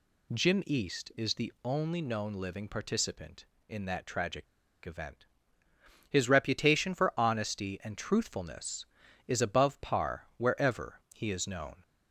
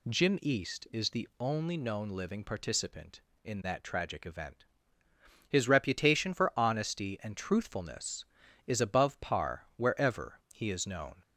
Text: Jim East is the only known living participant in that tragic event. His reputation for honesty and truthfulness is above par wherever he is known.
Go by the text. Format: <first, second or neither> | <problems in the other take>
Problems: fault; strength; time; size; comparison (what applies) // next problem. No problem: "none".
second | pauses between "tragic" and "event"; at 4.4 s; 0.40 s long